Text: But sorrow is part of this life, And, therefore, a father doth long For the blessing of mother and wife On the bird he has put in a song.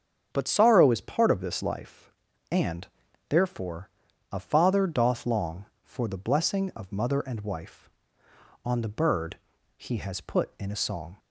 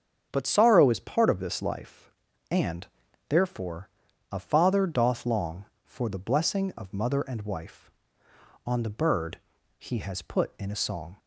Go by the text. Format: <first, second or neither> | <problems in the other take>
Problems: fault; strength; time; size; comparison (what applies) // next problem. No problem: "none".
neither | starts louder than the rest; strong; the same in both // pauses between "bird" and "he"; the same in both